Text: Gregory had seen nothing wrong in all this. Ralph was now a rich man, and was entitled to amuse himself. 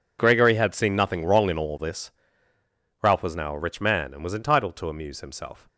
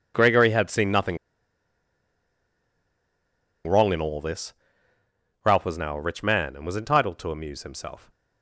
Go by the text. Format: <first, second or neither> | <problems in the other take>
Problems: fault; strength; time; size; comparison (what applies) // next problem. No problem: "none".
first | pauses between "nothing" and "wrong"; strong; at 1.1 s; 2.4 s long